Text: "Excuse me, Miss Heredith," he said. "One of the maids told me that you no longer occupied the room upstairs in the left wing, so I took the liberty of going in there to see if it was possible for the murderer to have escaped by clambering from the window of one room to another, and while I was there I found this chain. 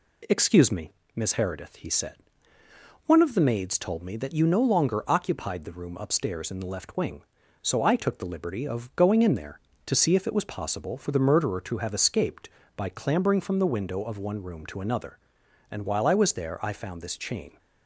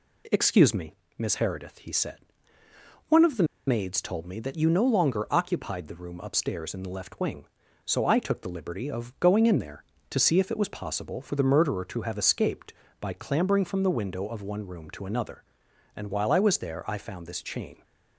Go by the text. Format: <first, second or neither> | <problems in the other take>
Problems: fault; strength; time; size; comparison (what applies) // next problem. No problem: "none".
first | pauses between "the" and "maids"; slight; at 3.4 s; 0.23 s long